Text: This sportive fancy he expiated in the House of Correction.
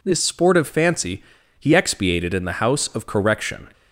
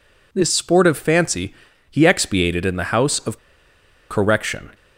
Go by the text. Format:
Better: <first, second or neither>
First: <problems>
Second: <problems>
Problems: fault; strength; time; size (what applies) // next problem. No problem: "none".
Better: first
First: pauses between "fancy" and "he"; slight; at 1.2 s; 0.36 s long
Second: pauses between "fancy" and "he"; slight; at 1.5 s; 0.36 s long // pauses between "of" and "Correction"; noticeable; at 3.3 s; 0.73 s long